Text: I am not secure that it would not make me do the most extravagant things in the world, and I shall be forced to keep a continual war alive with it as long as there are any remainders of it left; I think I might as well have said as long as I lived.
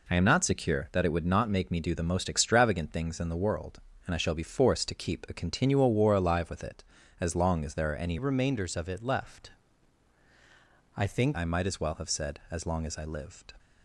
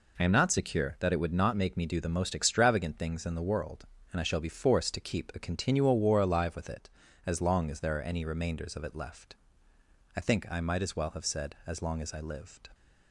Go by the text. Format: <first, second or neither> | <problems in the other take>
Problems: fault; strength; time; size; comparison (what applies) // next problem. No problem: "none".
second | changes voice from "remainders" to "think"; from 8.1 to 11.3 s; 3.2 s long